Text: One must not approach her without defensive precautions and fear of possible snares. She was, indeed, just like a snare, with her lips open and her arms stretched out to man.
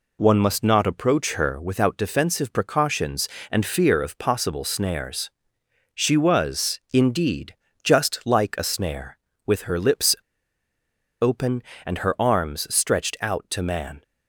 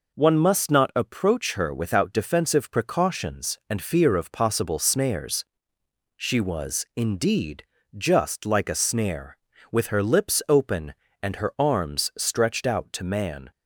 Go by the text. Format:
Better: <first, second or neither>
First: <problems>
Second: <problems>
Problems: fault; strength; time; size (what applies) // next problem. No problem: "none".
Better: second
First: pauses between "lips" and "open"; at 10.1 s; 1.0 s long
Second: none